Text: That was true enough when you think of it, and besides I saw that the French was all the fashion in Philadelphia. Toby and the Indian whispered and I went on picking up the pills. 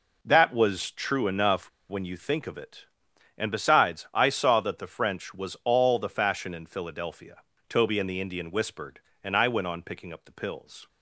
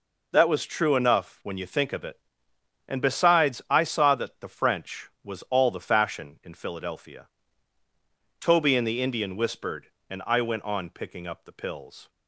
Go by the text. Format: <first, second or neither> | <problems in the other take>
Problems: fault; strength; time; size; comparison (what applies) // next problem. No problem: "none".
second | pauses between "enough" and "when"; slight; at 1.6 s; 0.20 s long